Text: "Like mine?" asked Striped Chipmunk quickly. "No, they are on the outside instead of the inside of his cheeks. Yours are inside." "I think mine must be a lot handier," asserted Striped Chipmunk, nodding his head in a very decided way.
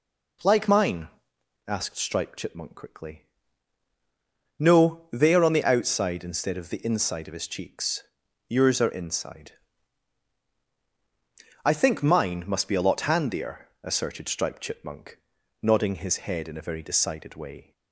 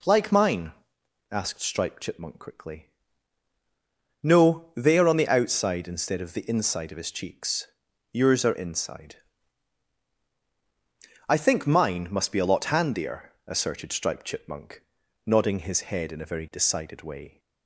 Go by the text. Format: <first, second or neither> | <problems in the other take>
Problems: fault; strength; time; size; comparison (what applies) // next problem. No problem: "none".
neither | none